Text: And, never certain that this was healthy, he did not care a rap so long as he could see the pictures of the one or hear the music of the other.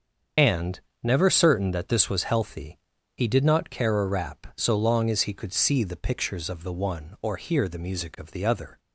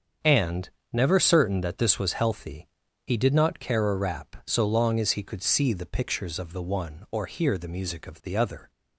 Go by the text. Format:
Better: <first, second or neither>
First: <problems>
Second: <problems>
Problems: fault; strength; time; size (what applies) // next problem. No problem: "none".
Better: second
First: loses the start of "And"; at 0.3 s; 45 ms // starts louder than the rest; until 1.6 s; 7 dB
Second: starts louder than the rest; strong; until 1.4 s; 7 dB